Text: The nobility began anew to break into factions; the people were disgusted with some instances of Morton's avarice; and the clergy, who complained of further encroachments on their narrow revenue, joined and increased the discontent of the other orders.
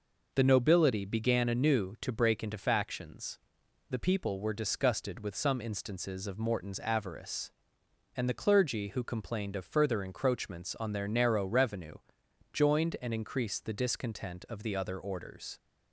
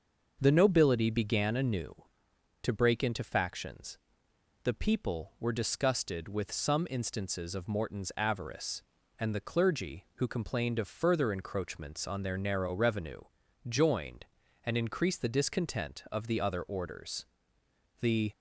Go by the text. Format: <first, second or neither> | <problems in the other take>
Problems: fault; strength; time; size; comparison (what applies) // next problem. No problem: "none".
first | starts louder than the rest; until 1.4 s; 6.5 dB // goes on to say "The"; slight; from 17.9 s on; 0.32 s long